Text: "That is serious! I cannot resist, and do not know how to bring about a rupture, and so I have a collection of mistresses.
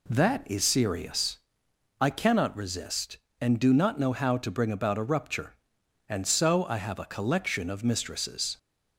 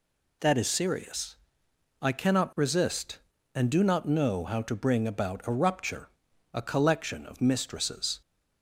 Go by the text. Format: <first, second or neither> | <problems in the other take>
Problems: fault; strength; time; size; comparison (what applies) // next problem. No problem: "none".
first | skips "and so I have"; at 6.3 s